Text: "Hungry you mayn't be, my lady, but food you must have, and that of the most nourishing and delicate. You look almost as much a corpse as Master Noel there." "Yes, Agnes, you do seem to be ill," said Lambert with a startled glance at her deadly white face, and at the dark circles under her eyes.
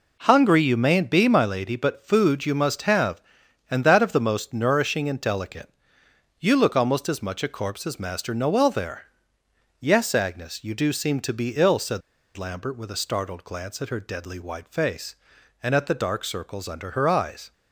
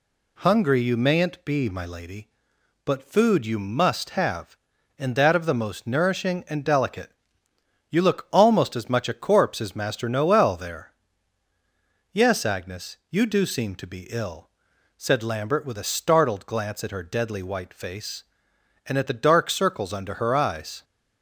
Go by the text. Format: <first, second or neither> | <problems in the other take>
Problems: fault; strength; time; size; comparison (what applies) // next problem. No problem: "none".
second | pauses between "said" and "Lambert"; slight; at 12.0 s; 0.34 s long